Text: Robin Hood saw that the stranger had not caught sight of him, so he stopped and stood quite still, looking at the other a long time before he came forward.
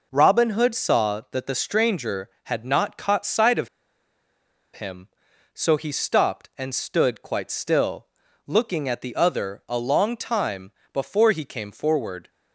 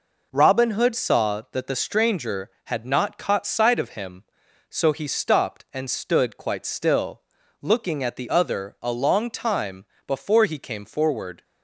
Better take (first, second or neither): second